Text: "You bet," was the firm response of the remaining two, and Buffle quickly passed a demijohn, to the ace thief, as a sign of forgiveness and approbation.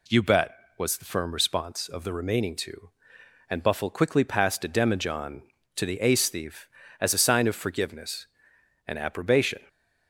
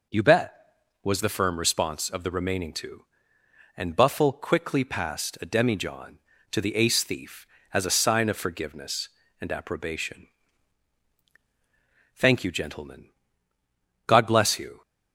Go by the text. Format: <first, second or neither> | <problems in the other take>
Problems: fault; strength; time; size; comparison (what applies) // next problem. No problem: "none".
first | goes on to say "Thank you gentlemen God bless you"; strong; from 12.1 s on; 2.6 s long